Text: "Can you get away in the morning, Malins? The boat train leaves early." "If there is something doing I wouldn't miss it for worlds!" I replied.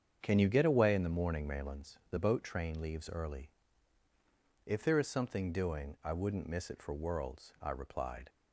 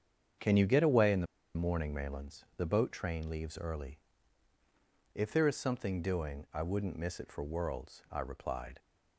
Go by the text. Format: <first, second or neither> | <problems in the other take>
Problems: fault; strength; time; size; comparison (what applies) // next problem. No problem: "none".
first | starts louder than the rest; strong; until 1.7 s; 7.5 dB; strong in the first // pauses between "the" and "morning"; slight; at 1.2 s; 0.30 s long